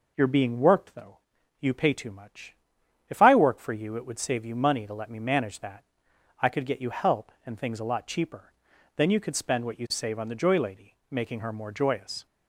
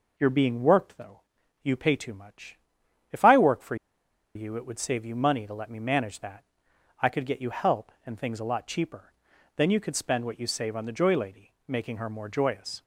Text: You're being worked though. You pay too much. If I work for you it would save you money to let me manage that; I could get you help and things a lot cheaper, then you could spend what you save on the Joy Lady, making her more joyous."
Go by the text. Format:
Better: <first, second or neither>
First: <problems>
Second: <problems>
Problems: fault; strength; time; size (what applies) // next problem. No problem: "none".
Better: first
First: none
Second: pauses between "for" and "you"; noticeable; at 3.7 s; 0.60 s long